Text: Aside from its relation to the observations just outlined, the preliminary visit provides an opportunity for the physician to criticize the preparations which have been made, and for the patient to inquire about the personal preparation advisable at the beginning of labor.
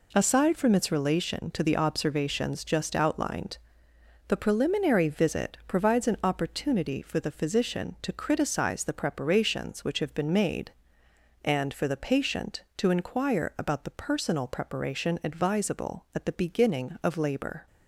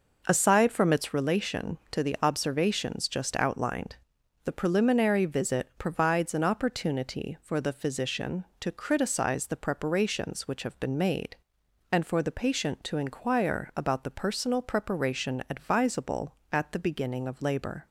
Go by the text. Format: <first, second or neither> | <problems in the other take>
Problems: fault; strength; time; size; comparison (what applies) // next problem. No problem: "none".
first | starts louder than the rest; noticeable; until 1.2 s; 5.5 dB